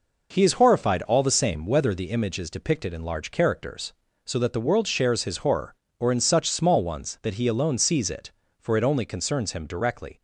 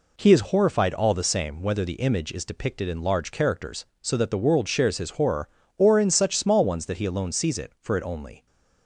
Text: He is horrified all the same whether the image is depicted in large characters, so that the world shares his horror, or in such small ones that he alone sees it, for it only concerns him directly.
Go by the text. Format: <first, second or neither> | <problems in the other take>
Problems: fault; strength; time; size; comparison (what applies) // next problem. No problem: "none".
first | stops before "concerns him directly"; at 8.4 s